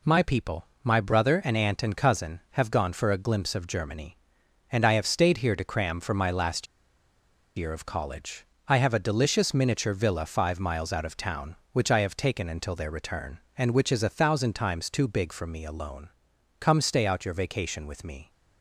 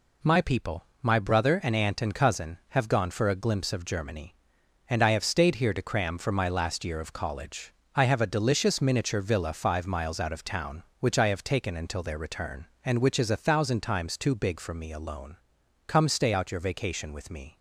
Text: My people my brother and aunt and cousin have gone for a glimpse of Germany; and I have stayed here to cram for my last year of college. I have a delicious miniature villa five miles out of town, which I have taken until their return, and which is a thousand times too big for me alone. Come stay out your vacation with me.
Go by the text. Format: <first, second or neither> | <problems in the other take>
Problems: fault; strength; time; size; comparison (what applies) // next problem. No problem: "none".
second | pauses between "people" and "my"; slight; at 0.6 s; 0.20 s long; slight in the second // pauses between "last" and "year"; noticeable; at 6.6 s; 0.91 s long